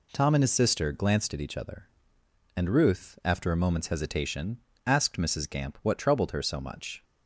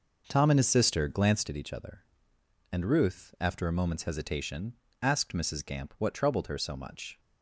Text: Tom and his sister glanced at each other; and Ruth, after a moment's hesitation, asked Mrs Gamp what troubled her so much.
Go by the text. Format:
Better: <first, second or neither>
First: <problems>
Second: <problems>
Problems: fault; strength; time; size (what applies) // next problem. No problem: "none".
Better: first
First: none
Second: starts louder than the rest; noticeable; until 1.6 s; 5.5 dB